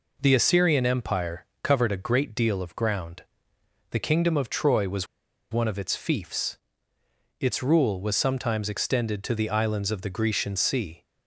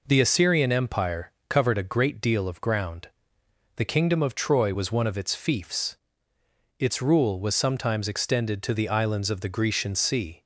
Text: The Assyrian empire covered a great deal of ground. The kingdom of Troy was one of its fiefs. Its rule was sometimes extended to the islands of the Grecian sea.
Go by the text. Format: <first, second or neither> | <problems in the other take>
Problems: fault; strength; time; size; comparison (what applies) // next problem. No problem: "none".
second | pauses between "empire" and "covered"; slight; at 1.4 s; 0.16 s long; slight in the second // pauses between "was" and "one"; noticeable; at 5.0 s; 0.46 s long